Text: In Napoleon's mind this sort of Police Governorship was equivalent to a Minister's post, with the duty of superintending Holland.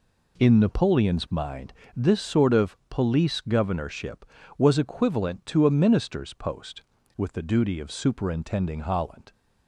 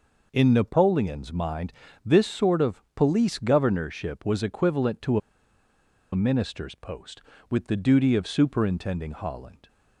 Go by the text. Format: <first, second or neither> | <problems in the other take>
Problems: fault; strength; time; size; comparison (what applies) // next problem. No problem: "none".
first | pauses between "mind" and "this"; slight; at 1.7 s; 0.32 s long; slight in the first // pauses between "to" and "a"; noticeable; at 5.1 s; 0.95 s long